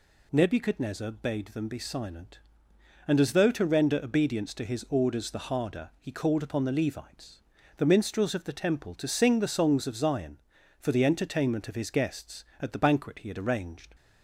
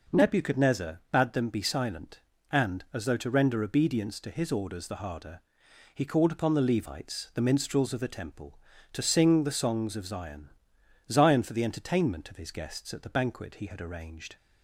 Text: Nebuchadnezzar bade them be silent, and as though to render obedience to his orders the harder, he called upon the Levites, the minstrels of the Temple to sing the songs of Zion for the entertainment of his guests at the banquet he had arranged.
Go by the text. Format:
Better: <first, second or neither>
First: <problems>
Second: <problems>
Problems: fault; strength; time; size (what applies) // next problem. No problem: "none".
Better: first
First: none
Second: says "Zion" twice; at 11.1 s